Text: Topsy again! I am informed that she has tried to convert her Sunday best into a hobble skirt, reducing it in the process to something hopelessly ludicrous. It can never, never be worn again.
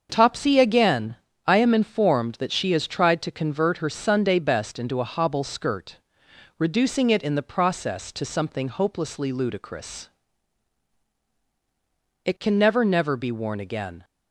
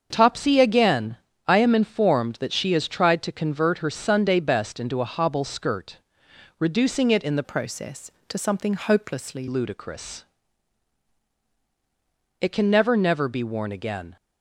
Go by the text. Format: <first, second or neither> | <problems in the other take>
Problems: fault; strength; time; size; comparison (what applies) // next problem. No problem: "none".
first | starts louder than the rest; until 1.1 s; 7 dB; also in the first // changes voice from "process" to "hopelessly"; from 7.4 to 9.4 s; 2.0 s long